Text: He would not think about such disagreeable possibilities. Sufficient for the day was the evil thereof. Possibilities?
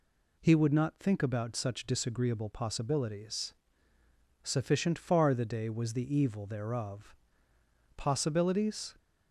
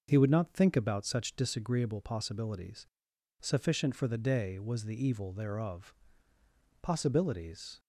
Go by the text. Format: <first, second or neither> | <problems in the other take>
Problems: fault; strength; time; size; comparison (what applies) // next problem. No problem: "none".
second | says "far" for "for"; at 4.9 s